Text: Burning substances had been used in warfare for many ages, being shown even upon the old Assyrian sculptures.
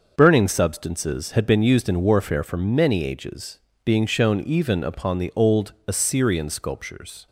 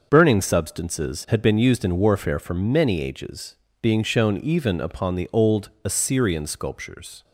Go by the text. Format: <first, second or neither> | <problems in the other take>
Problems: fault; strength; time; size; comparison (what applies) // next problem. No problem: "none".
neither | starts louder than the rest; noticeable; the same in both